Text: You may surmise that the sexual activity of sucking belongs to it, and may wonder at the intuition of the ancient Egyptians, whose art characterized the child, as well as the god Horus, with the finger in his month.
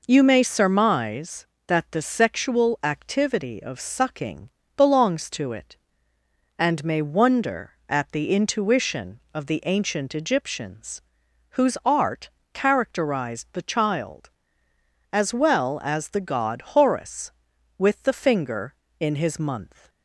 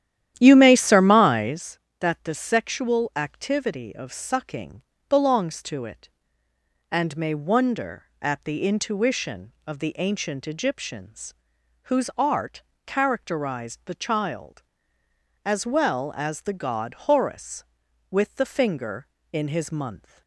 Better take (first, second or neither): first